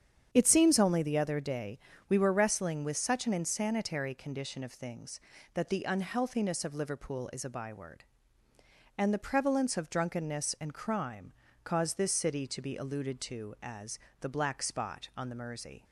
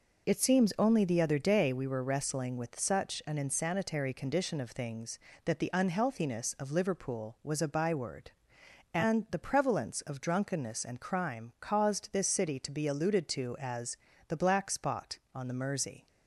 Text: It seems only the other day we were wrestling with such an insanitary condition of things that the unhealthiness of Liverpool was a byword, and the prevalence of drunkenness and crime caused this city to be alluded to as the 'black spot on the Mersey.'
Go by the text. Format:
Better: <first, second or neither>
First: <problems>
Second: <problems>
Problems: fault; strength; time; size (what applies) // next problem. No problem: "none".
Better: second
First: starts louder than the rest; strong; until 1.3 s; 8 dB // pauses between "day" and "we"; slight; at 1.7 s; 0.30 s long // says "is" for "was"; at 7.3 s // pauses between "crime" and "caused"; slight; at 11.3 s; 0.32 s long // pauses between "as" and "the"; slight; at 13.9 s; 0.22 s long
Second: pauses between "as" and "the"; slight; at 13.9 s; 0.32 s long